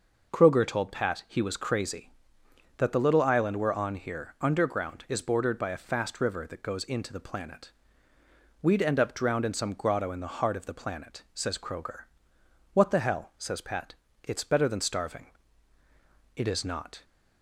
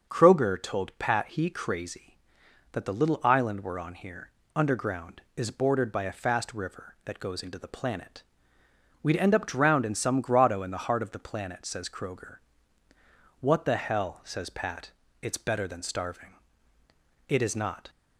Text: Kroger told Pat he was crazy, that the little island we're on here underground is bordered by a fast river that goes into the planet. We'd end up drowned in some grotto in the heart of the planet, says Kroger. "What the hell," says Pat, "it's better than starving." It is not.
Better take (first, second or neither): first